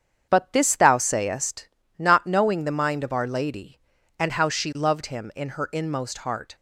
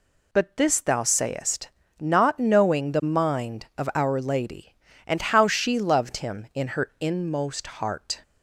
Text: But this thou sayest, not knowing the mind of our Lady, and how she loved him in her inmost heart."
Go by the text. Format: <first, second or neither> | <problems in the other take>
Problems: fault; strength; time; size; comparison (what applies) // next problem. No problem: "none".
second | starts louder than the rest; strong; until 1.8 s; 8 dB